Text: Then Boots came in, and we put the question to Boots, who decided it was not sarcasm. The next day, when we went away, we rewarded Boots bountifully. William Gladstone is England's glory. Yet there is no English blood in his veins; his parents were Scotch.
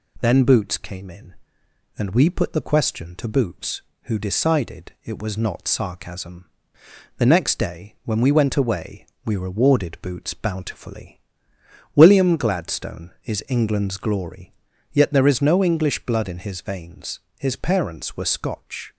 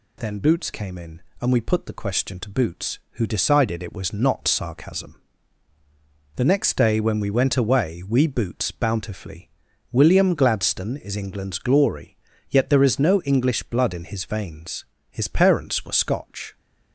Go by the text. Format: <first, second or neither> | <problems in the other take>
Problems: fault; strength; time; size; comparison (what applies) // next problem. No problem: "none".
first | skips "rewarded"; at 8.2 s